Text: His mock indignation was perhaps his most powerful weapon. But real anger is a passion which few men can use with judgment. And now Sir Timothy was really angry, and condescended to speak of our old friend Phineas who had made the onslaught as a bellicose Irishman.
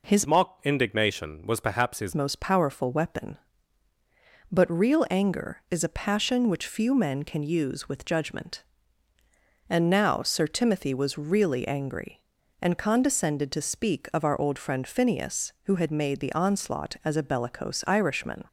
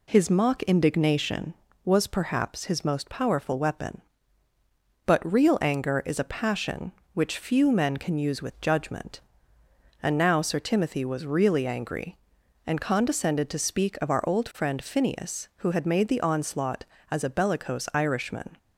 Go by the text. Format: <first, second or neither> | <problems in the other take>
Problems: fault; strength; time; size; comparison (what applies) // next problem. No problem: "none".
second | changes voice from "mock" to "his"; from 0.2 to 2.1 s; 1.9 s long